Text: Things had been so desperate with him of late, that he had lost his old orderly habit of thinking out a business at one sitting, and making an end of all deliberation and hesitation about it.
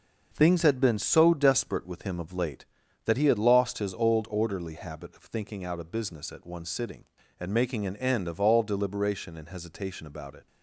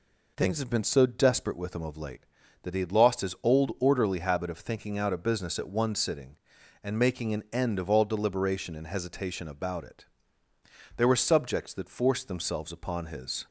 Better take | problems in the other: first | goes on to say "There were subjects that forced themselves upon his"; strong; from 10.9 s on; 2.5 s long

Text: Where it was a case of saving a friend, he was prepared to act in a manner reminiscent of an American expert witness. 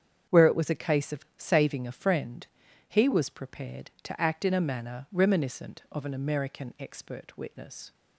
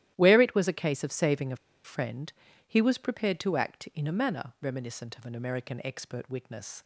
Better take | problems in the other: first | starts louder than the rest; strong; until 1.1 s; 13 dB; strong in the first // pauses between "a" and "friend"; slight; at 1.5 s; 0.28 s long

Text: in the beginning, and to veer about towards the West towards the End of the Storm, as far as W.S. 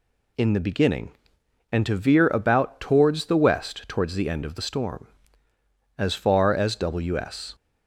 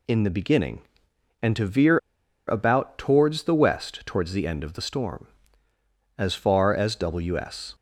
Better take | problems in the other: first | pauses between "veer" and "about"; noticeable; at 1.9 s; 0.50 s long

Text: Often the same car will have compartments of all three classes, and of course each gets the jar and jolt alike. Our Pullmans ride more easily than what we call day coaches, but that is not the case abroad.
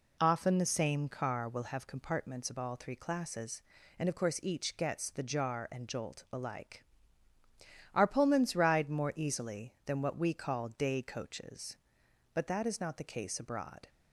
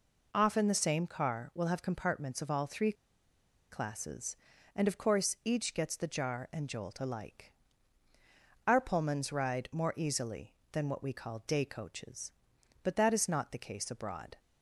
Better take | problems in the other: first | pauses between "three" and "classes"; noticeable; at 2.9 s; 0.78 s long

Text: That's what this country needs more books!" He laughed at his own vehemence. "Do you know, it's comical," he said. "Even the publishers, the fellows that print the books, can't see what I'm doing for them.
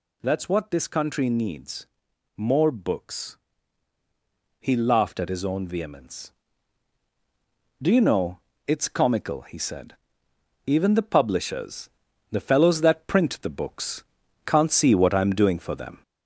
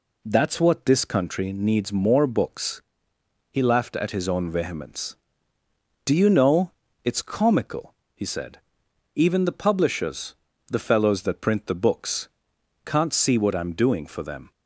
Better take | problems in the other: second | gets louder; throughout; 4 dB // pauses between "needs" and "more"; noticeable; at 1.8 s; 0.50 s long

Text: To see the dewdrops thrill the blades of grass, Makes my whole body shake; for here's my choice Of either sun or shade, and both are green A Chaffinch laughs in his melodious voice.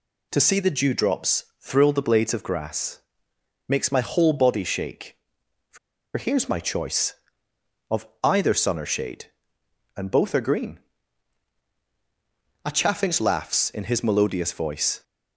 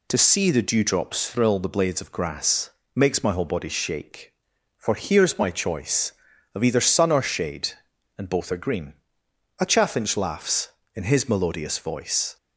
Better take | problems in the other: second | pauses between "dewdrops" and "thrill"; slight; at 1.4 s; 0.16 s long // pauses between "for" and "here's"; at 5.7 s; 0.38 s long // pauses between "Of" and "either"; slight; at 8.0 s; 0.16 s long // pauses between "green" and "A"; strong; at 10.7 s; 1.8 s long; noticeable in the second

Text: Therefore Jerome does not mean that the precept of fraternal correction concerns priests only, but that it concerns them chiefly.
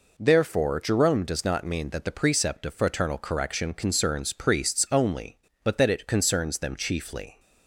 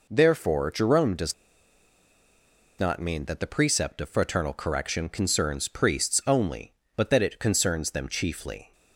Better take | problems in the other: first | pauses between "does" and "not"; strong; at 1.3 s; 1.4 s long

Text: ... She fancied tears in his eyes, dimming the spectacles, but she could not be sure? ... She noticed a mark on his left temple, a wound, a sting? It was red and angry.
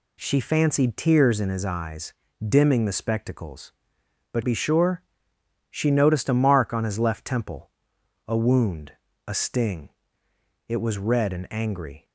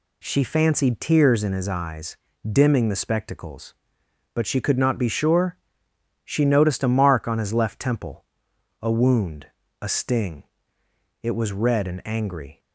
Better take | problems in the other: second | skips "she could not"; at 4.4 s

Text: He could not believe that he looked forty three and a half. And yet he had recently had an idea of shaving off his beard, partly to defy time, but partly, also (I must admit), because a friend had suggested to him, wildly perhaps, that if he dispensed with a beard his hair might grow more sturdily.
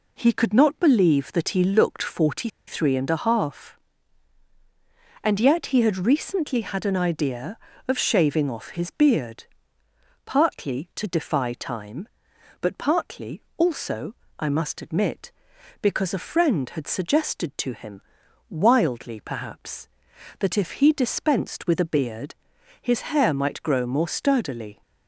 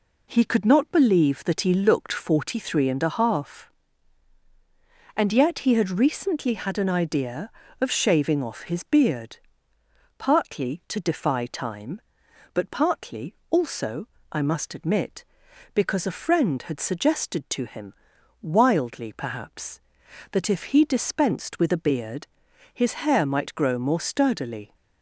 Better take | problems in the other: second | pauses between "forty" and "three"; slight; at 2.4 s; 0.19 s long // pauses between "beard" and "his"; noticeable; at 22.3 s; 0.48 s long; noticeable in the second

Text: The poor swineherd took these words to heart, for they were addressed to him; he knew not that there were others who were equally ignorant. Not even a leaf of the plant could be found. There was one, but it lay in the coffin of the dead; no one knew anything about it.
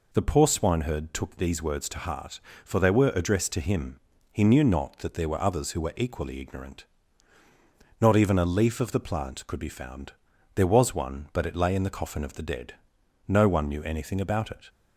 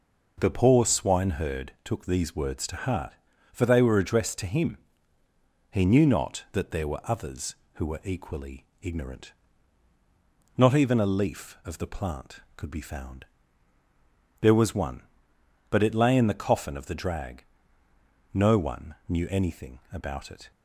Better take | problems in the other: first | pauses between "equally" and "ignorant"; slight; at 8.6 s; 0.16 s long // says "drag" for "dead"; at 16.9 s

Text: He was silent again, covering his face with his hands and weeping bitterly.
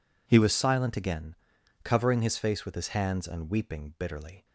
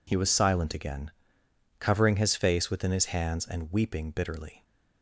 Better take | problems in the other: first | says "within" for "with"; at 2.7 s

